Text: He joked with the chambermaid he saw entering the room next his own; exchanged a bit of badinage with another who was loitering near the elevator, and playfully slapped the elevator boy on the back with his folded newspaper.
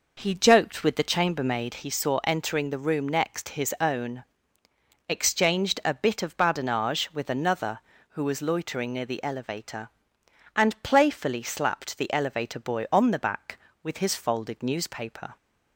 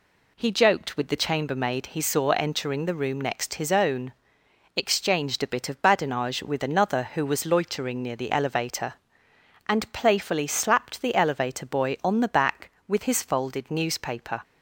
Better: second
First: starts louder than the rest; noticeable; until 1.8 s; 5 dB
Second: none

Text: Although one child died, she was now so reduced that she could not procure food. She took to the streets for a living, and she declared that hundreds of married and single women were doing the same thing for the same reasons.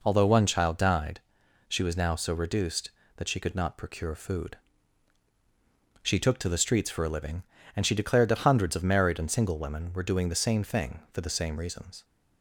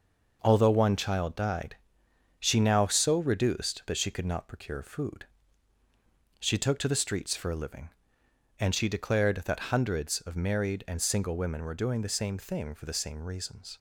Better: first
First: none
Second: skips "was"; at 2.6 s

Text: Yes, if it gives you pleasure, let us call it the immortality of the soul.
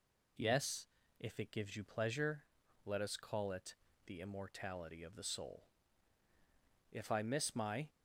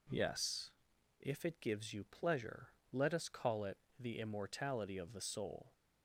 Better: second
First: pauses between "it" and "the"; slight; at 3.7 s; 0.30 s long // goes on to say "If I miss my"; noticeable; from 6.9 s on; 0.96 s long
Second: pauses between "it" and "the"; slight; at 3.7 s; 0.24 s long

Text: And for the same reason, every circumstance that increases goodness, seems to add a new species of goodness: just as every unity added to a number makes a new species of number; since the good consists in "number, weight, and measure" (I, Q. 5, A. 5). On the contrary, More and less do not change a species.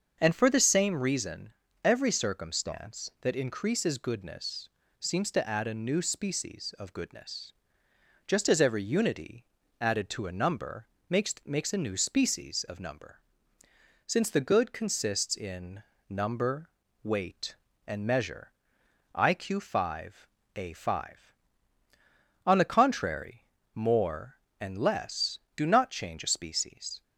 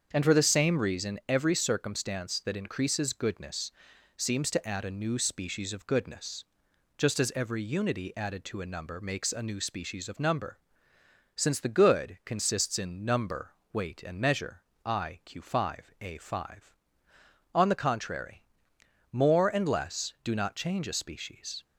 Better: second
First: starts louder than the rest; until 1.2 s; 6.5 dB // pauses between "unity" and "added"; slight; at 9.4 s; 0.36 s long // pauses between "number" and "makes"; slight; at 10.8 s; 0.20 s long // says "makes" twice; at 11.4 s // pauses between "in" and "number"; slight; at 15.8 s; 0.24 s long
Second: starts louder than the rest; until 1.1 s; 7 dB

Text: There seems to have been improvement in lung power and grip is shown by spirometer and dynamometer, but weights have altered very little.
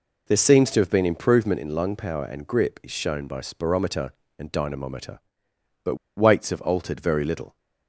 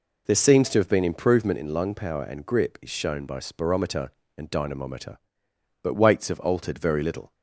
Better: second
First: pauses between "but" and "weights"; slight; at 5.9 s; 0.21 s long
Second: none

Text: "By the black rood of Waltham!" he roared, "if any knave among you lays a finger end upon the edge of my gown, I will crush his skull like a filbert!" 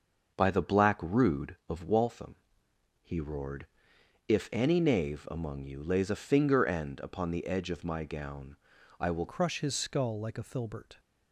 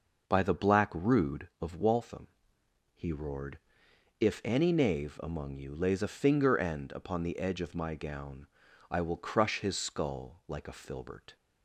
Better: second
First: starts louder than the rest; until 1.4 s; 6.5 dB // changes voice at "crush"; from 9.2 s on; 1.7 s long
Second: none

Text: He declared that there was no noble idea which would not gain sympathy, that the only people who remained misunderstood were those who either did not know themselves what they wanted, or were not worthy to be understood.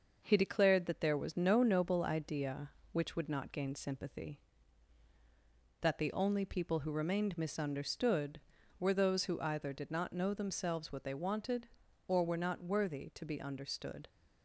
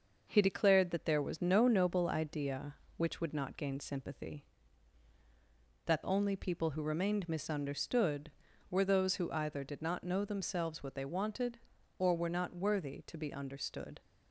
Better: first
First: none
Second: skips "the"; at 6.0 s

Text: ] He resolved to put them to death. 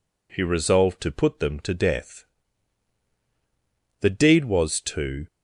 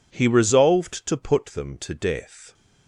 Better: second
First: goes on to say "The deed was to"; noticeable; from 3.9 s on; 1.2 s long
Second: none

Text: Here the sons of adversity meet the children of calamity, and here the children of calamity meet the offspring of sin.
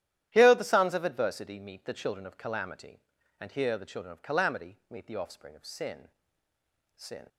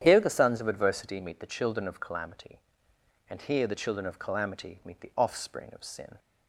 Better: second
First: starts louder than the rest; strong; until 1.3 s; 12 dB // says "sin" twice; at 6.9 s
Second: starts louder than the rest; strong; until 1.0 s; 9.5 dB

